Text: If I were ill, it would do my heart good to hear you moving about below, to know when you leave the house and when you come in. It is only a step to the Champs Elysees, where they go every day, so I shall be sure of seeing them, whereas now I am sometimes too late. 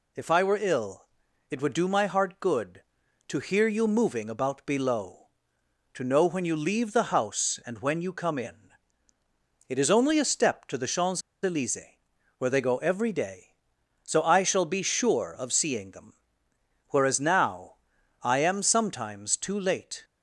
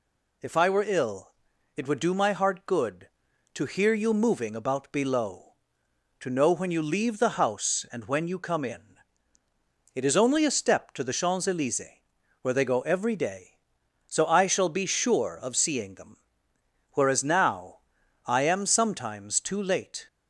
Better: second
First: pauses between "Champs" and "Elysees"; slight; at 11.2 s; 0.23 s long // pauses between "now" and "I"; noticeable; at 17.7 s; 0.50 s long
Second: pauses between "now" and "I"; noticeable; at 17.7 s; 0.50 s long

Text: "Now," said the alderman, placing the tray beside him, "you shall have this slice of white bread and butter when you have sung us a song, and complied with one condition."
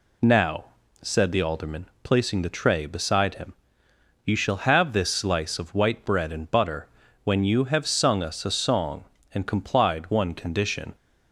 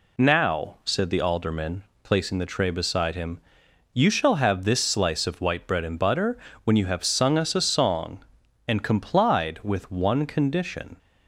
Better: second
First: pauses between "butter" and "when"; at 6.8 s; 0.38 s long // skips "with"; at 10.0 s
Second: pauses between "butter" and "when"; slight; at 6.3 s; 0.28 s long

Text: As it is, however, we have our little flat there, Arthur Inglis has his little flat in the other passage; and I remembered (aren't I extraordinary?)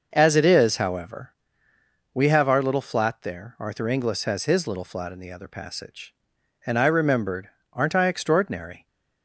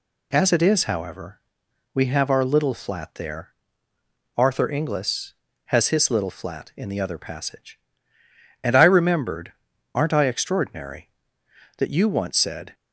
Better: first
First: none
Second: goes on to say "that you once said"; noticeable; from 11.7 s on; 0.94 s long

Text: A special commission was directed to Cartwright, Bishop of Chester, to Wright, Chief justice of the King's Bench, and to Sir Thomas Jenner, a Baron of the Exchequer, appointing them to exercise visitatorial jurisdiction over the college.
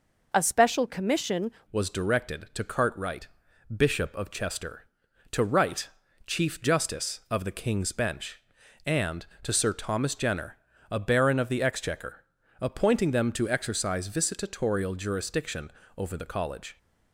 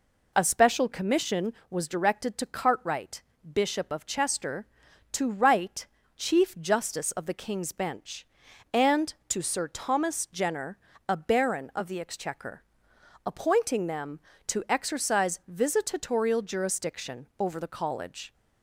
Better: second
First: changes voice at "was"; from 1.7 s on; 15.0 s long // pauses between "jurisdiction" and "over"; slight; at 15.7 s; 0.24 s long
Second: none

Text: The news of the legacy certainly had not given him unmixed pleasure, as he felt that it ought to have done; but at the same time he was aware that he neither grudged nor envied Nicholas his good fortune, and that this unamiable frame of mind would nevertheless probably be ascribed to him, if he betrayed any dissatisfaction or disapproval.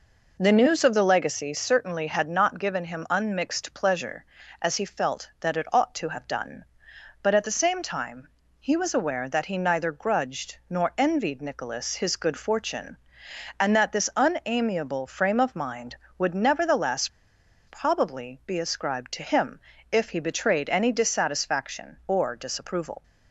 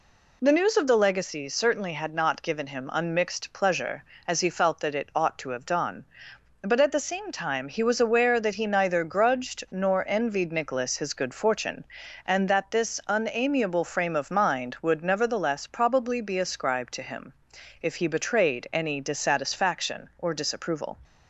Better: second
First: pauses between "time" and "he"; slight; at 8.2 s; 0.32 s long // pauses between "nevertheless" and "probably"; noticeable; at 17.0 s; 0.59 s long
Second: none

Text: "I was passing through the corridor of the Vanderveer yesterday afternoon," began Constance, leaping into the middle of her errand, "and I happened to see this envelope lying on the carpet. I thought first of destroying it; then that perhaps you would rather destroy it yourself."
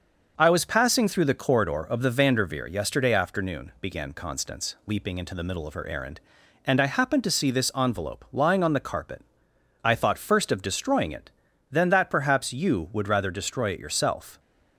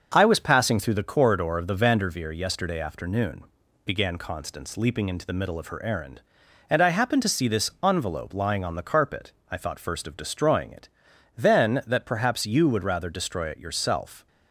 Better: neither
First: starts louder than the rest; until 1.3 s; 6.5 dB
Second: starts louder than the rest; until 1.1 s; 6 dB

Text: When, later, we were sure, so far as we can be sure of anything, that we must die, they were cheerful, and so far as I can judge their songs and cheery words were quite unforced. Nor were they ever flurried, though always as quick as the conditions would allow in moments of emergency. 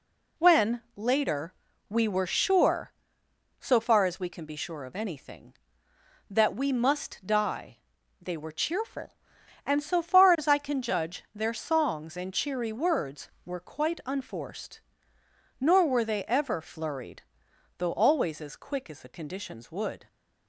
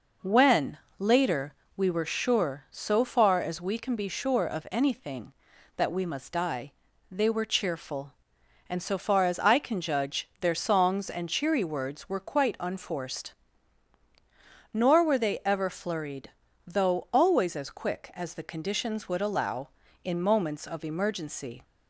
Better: second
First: stops before "allow in moments of emergency"; at 20.0 s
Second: none

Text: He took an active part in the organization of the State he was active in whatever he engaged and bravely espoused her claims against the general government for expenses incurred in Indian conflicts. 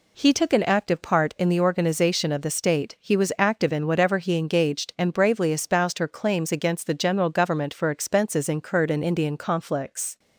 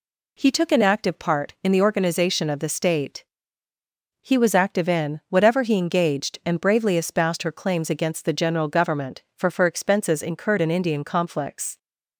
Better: first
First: none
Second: pauses between "State" and "he"; noticeable; at 3.2 s; 0.96 s long // says "for" twice; at 9.4 s

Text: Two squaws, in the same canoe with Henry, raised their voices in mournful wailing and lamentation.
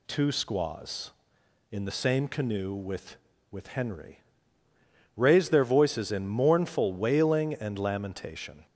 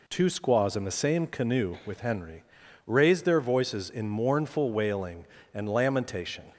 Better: second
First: says "with" twice; at 3.5 s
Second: none

